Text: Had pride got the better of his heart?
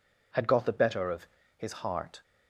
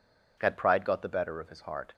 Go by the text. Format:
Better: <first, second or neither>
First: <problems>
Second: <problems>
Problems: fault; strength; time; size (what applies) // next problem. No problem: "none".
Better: second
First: skips "pride"; at 0.4 s // pauses between "of" and "his"; slight; at 1.2 s; 0.32 s long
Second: none